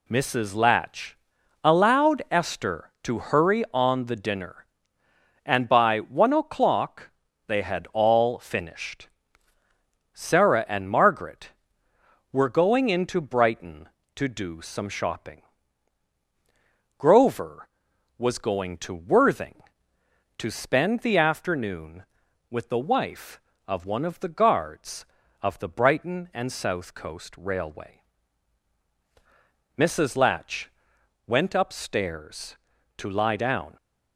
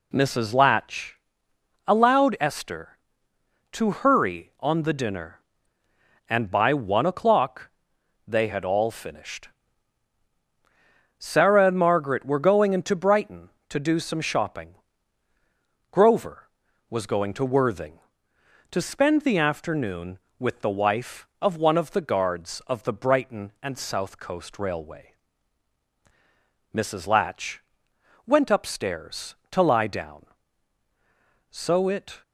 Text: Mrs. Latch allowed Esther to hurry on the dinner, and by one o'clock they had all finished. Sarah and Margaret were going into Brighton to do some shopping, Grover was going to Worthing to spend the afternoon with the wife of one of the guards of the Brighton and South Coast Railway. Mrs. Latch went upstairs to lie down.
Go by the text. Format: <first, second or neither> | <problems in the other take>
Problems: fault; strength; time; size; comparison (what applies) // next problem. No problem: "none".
first | pauses between "Latch" and "allowed"; noticeable; at 1.1 s; 0.72 s long; noticeable in the first // pauses between "o'clock" and "they"; noticeable; at 7.7 s; 0.58 s long; also in the first // pauses between "Latch" and "went"; noticeable; at 27.6 s; 0.64 s long; noticeable in the first // goes on to say "So it"; noticeable; from 31.5 s on; 0.72 s long